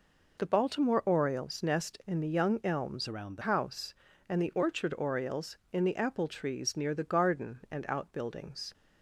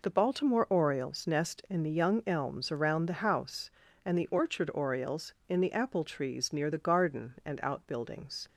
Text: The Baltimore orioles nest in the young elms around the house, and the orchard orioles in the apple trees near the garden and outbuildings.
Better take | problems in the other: second | changes voice from "around" to "the"; from 3.0 to 3.4 s; 0.4 s long

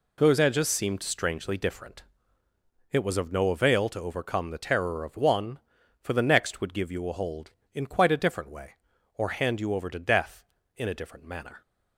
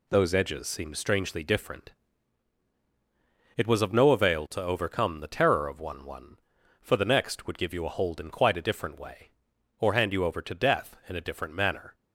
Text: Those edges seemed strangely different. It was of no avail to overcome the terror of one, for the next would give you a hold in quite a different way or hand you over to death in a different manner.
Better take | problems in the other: first | says "one" twice; at 6.0 s

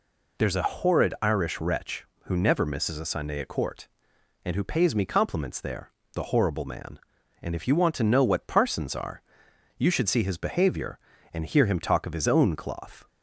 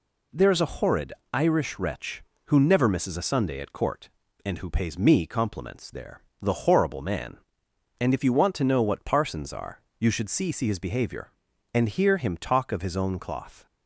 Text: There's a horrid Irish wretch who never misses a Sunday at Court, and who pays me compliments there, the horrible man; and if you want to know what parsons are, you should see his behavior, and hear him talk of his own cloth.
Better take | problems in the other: first | pauses between "horrid" and "Irish"; slight; at 1.1 s; 0.22 s long // says "see" twice; at 10.5 s

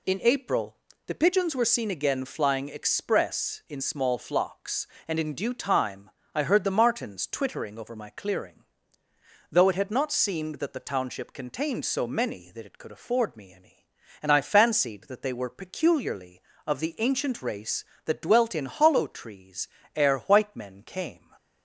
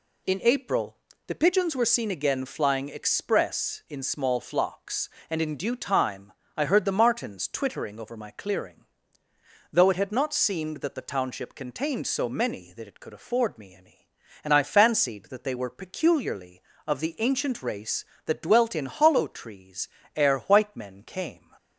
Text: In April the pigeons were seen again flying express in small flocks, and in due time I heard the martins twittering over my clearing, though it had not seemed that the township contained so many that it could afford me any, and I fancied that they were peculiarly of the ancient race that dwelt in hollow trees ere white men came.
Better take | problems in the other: neither | pauses between "April" and "the"; slight; the same in both // pauses between "time" and "I"; slight; the same in both // pauses between "trees" and "ere"; slight; the same in both

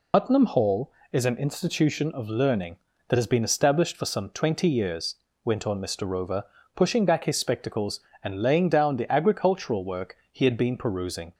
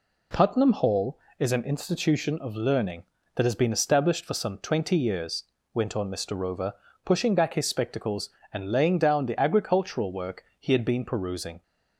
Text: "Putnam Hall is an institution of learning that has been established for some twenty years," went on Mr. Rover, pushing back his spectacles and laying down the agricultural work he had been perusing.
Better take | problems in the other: second | loses the start of "Putnam"; at 0.1 s; 100 ms // pauses between "work" and "he"; slight; at 10.1 s; 0.16 s long; slight in the second

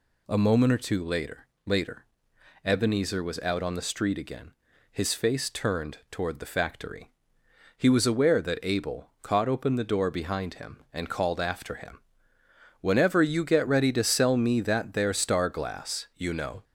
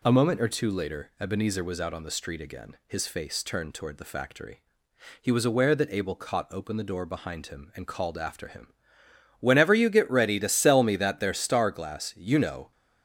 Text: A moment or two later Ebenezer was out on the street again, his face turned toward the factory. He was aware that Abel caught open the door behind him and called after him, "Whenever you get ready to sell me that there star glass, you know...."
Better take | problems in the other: second | says "later" twice; at 1.6 s

